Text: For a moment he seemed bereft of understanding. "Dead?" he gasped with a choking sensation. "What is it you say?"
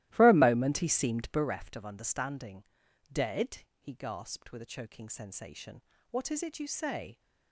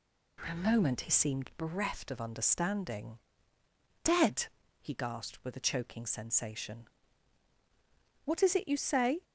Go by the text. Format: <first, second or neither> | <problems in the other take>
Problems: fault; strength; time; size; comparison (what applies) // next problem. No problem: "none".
second | starts louder than the rest; strong; until 1.5 s; 15.5 dB